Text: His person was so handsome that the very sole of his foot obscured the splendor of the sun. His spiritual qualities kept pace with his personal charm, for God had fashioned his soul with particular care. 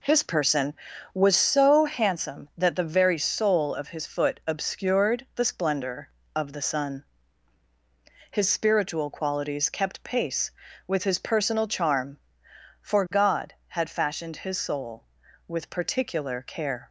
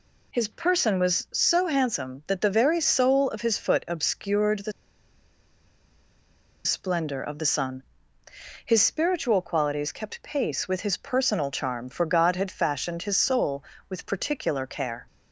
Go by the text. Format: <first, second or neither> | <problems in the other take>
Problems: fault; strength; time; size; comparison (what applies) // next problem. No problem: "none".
first | pauses between "the" and "splendor"; strong; at 4.7 s; 1.9 s long